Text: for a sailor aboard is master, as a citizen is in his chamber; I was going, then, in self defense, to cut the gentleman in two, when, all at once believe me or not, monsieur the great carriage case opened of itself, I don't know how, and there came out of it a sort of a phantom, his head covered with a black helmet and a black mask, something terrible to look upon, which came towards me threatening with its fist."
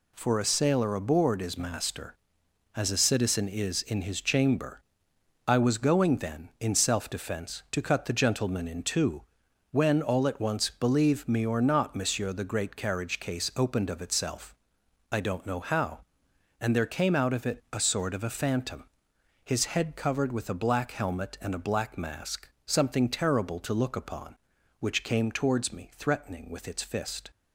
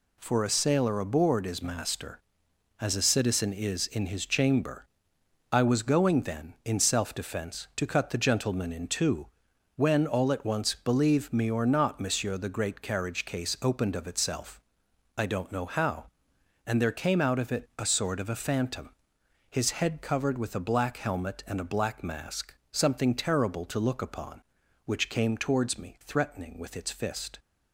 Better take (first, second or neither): neither